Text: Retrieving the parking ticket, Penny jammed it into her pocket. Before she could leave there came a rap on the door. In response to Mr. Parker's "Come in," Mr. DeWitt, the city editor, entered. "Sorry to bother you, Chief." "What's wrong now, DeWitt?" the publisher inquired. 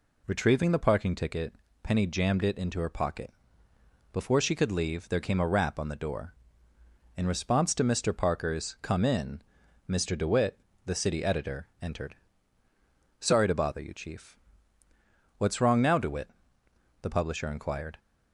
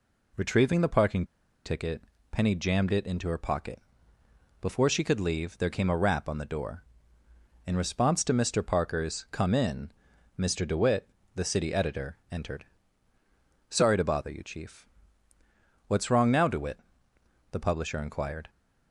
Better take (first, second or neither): first